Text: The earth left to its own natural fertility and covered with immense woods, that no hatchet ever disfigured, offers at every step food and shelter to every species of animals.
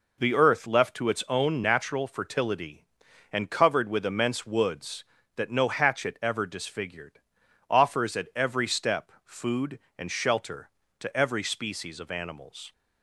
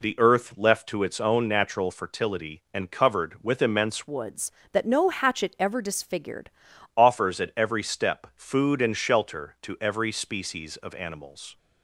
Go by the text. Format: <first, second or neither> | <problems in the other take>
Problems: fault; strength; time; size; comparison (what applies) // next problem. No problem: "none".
first | changes voice from "woods" to "disfigured"; from 4.0 to 6.4 s; 2.4 s long